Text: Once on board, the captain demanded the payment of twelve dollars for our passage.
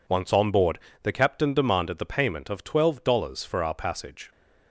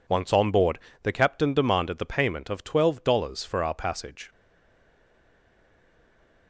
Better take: first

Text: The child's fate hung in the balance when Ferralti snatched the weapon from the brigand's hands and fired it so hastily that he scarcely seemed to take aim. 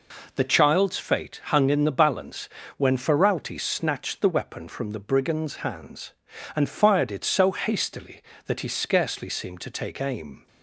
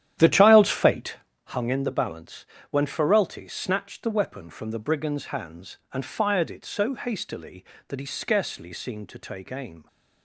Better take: first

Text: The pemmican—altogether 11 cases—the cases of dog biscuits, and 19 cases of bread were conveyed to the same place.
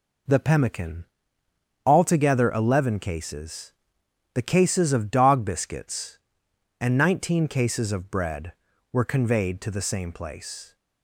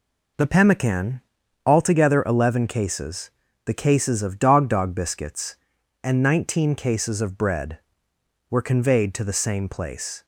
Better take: first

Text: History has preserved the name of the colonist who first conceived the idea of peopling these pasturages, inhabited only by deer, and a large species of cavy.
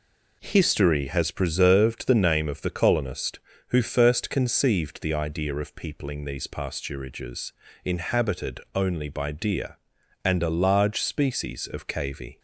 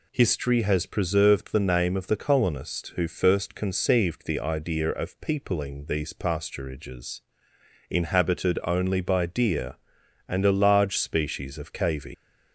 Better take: first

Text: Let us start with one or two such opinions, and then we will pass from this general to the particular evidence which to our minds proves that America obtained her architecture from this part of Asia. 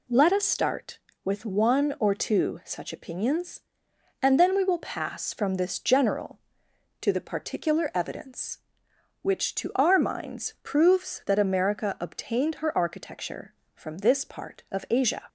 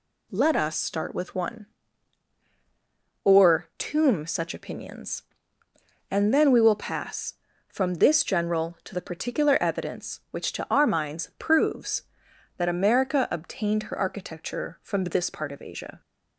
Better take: first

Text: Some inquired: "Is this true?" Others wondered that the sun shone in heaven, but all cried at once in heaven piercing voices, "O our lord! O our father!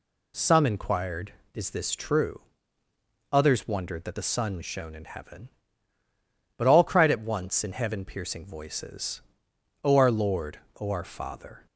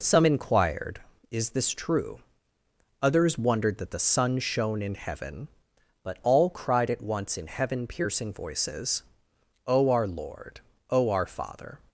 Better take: neither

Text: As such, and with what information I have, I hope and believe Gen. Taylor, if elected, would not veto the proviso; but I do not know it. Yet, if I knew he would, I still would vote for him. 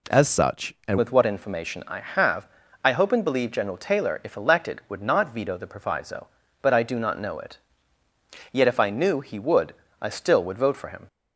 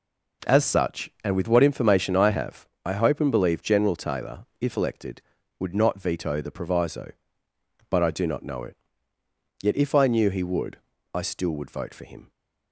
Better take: second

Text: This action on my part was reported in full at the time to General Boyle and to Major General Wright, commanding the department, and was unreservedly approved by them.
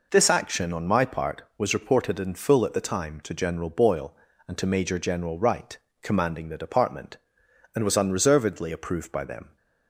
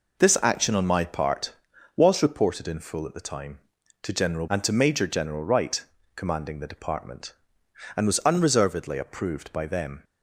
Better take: first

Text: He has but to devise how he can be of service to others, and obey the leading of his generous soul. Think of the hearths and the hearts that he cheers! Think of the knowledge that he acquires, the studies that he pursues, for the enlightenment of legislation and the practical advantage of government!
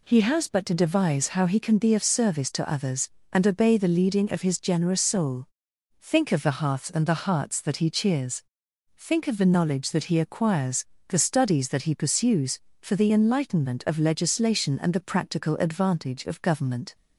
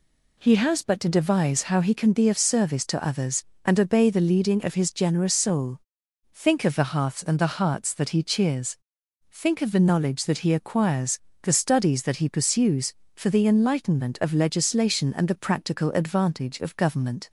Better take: neither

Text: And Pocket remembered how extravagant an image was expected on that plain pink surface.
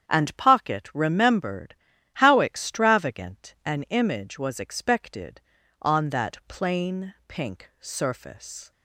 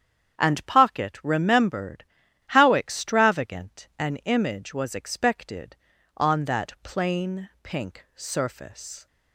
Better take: neither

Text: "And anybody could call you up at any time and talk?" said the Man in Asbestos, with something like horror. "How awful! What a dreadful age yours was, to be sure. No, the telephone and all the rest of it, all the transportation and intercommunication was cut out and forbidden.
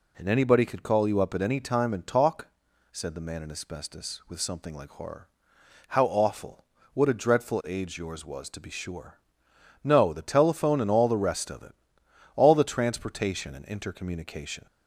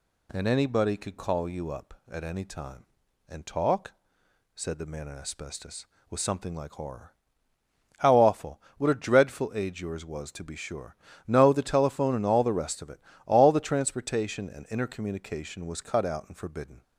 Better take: second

